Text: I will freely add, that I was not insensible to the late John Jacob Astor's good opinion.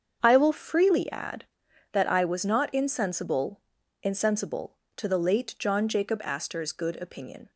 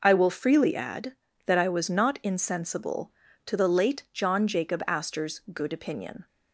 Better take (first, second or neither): second